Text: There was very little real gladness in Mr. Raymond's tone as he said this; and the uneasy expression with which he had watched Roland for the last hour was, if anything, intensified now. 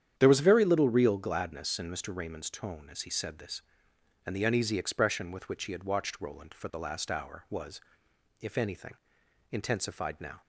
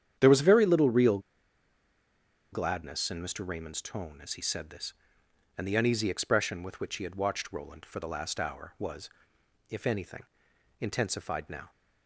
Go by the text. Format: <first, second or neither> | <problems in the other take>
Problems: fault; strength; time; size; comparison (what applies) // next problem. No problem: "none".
first | starts louder than the rest; strong; until 1.2 s; 9 dB; strong in the first // pauses between "real" and "gladness"; strong; at 1.1 s; 1.3 s long